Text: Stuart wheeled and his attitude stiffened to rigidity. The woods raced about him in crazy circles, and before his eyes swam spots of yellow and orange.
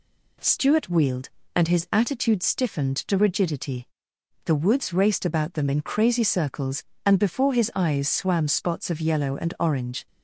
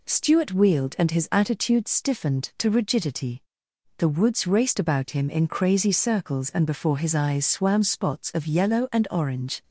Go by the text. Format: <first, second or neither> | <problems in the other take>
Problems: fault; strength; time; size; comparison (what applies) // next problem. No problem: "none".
second | says "them" for "him"; at 5.5 s